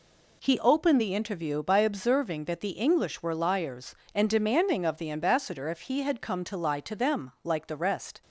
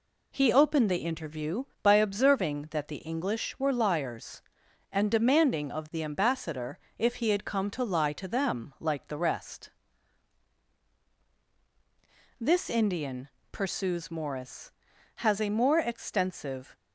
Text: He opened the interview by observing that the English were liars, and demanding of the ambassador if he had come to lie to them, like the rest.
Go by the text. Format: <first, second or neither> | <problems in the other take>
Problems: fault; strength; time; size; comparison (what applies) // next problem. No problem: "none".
first | pauses between "ambassador" and "if"; slight; at 6.7 s; 0.22 s long // goes on to say "This Indian pursues Morris has a more extensive"; strong; from 12.4 s on; 4.3 s long